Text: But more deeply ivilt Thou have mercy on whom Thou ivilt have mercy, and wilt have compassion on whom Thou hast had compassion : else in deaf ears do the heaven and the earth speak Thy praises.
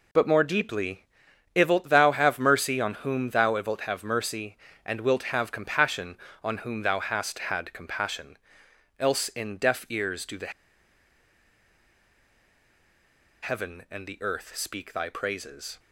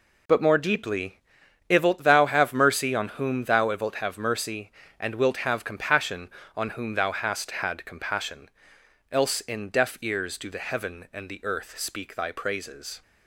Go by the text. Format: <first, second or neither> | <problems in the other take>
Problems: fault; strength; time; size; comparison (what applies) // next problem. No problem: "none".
second | pauses between "deeply" and "ivilt"; noticeable; at 1.0 s; 0.50 s long; noticeable in the second // pauses between "the" and "heaven"; strong; at 10.5 s; 2.9 s long